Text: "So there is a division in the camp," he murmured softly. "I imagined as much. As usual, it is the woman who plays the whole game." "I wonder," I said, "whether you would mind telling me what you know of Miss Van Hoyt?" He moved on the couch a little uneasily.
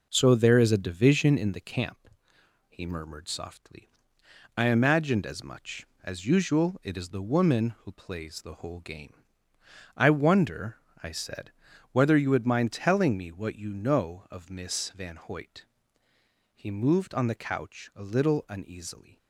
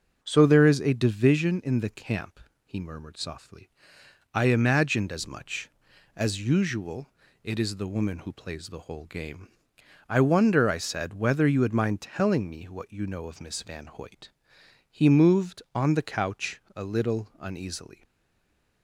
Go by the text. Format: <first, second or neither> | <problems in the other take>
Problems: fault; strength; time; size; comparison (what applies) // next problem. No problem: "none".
first | starts louder than the rest; until 1.2 s; 6.5 dB // stays silent after the last word; slight; from 18.0 s on; 0.8 s long